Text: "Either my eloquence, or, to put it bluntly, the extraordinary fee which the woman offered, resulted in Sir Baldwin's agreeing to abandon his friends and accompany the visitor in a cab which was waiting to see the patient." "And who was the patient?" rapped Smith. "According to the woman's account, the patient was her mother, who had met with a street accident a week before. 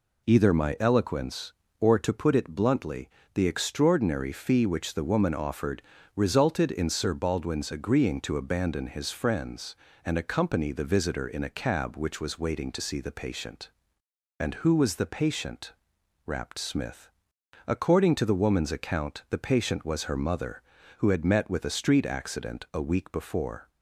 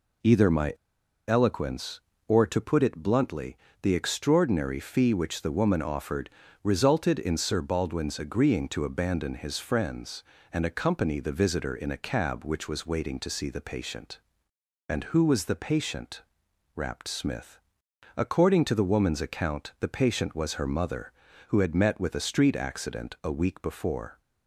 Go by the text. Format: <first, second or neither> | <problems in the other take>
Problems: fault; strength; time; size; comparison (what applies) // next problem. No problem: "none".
first | pauses between "my" and "eloquence"; noticeable; at 0.7 s; 0.53 s long